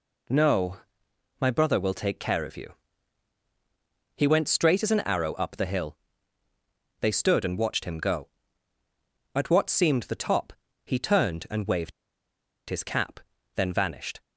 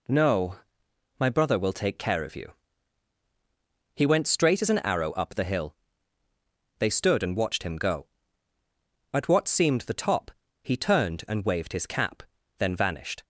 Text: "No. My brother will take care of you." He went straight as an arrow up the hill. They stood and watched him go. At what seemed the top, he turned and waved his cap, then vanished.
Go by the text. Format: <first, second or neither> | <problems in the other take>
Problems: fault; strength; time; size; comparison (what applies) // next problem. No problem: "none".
second | pauses between "waved" and "his"; noticeable; at 11.9 s; 0.77 s long